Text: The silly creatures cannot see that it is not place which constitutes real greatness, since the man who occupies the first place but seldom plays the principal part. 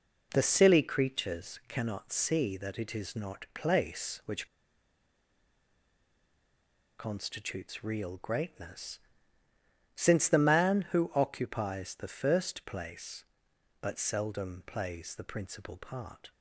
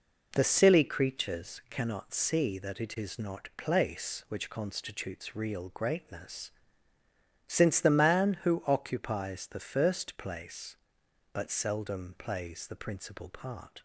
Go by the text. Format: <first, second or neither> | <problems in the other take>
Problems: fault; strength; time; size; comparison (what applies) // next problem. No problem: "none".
second | pauses between "which" and "constitutes"; strong; at 4.4 s; 2.5 s long